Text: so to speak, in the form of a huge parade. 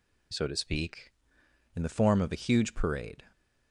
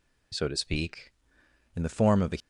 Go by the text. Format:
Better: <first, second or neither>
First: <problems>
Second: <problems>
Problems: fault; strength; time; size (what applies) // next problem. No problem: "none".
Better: first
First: none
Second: stops before "huge parade"; at 2.4 s